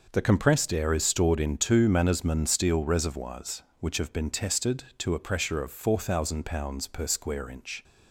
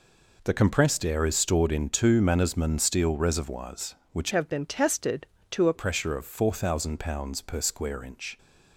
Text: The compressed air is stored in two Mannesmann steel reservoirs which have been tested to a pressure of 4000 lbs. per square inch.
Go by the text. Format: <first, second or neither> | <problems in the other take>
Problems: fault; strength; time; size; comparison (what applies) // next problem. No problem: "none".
first | changes voice from "have" to "a"; from 4.3 to 5.7 s; 1.4 s long